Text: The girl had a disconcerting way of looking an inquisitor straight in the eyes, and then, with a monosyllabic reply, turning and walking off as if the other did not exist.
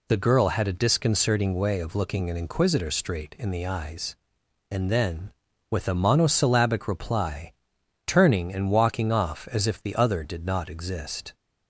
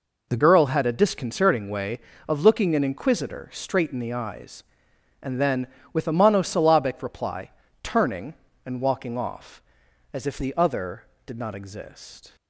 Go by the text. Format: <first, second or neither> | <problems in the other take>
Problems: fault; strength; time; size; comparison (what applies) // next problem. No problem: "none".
first | changes voice at "girl"; from 0.3 s on; 12.0 s long